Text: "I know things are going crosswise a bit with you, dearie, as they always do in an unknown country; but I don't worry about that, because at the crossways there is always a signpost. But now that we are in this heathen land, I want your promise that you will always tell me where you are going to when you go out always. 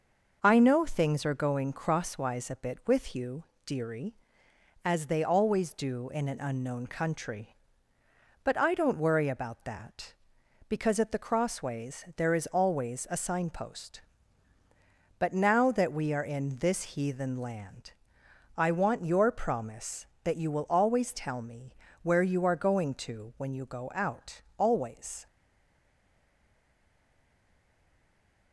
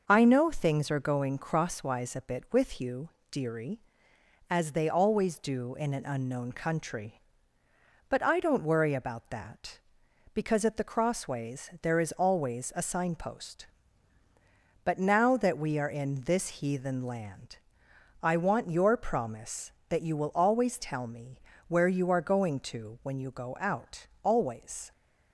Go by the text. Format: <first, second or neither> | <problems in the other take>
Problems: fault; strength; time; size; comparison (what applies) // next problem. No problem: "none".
second | starts louder than the rest; noticeable; until 1.4 s; 6 dB; noticeable in the second // pauses between "me" and "where"; slight; at 21.7 s; 0.28 s long; slight in the second // pauses between "out" and "always"; slight; at 24.3 s; 0.16 s long; slight in the second // stays silent after the last word; strong; from 25.2 s on; 3.3 s long